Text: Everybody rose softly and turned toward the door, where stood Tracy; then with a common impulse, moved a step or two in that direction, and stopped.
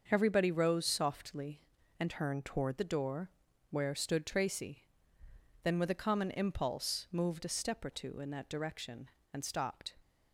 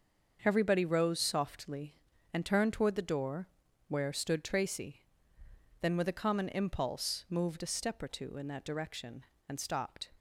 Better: second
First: starts louder than the rest; until 1.0 s; 6.5 dB // changes voice from "turned" to "toward"; from 2.0 to 2.7 s; 0.7 s long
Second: starts louder than the rest; until 1.4 s; 6.5 dB

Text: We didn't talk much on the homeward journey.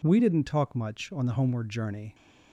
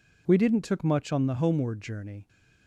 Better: first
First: none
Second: says "took" for "talk"; at 0.6 s

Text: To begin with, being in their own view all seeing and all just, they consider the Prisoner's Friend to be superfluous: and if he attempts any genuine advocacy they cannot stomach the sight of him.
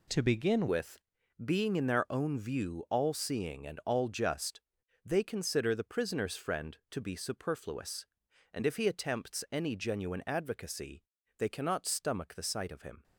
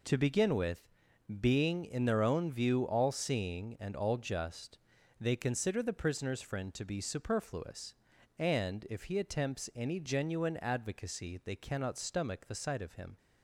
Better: second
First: changes voice at "with"; from 0.6 s on; 12.4 s long // pauses between "advocacy" and "they"; at 11.0 s; 0.38 s long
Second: none

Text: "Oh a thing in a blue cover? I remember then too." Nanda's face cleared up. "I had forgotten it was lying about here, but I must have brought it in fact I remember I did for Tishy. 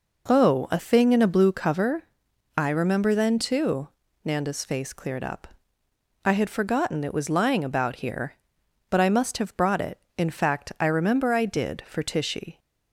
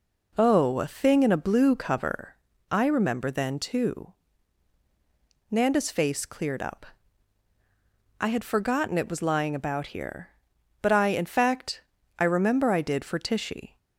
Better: first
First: none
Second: skips "must have brought it"; at 11.0 s // pauses between "fact" and "I"; slight; at 11.8 s; 0.36 s long

